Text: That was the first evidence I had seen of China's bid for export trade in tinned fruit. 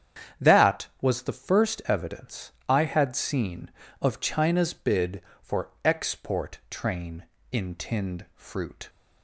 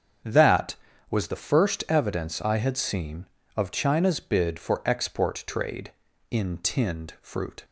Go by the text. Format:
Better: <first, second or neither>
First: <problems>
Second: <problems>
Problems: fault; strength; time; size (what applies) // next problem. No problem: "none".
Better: second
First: starts louder than the rest; strong; until 1.5 s; 8.5 dB // pauses between "evidence" and "I"; slight; at 2.5 s; 0.16 s long // pauses between "for" and "export"; slight; at 5.6 s; 0.16 s long // says "train" for "trade"; at 6.7 s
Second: starts louder than the rest; strong; until 1.6 s; 8 dB